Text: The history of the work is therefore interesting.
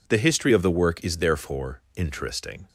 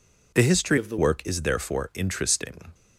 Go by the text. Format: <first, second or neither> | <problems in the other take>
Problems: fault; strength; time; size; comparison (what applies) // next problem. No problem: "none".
first | changes voice from "of" to "the"; from 0.7 to 0.9 s; 0.2 s long